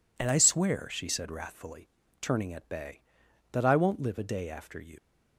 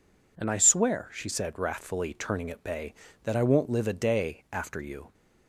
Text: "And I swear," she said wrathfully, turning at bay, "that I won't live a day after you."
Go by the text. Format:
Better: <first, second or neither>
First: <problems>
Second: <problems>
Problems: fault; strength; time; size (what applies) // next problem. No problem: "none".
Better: second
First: leaves "you" unfinished; at 4.9 s; 120 ms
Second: none